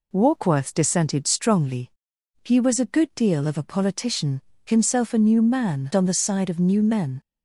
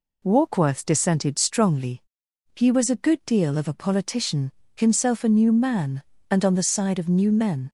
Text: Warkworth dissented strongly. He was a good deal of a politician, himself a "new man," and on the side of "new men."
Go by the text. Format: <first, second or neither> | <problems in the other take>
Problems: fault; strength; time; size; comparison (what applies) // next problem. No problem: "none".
second | skips "and"; at 5.9 s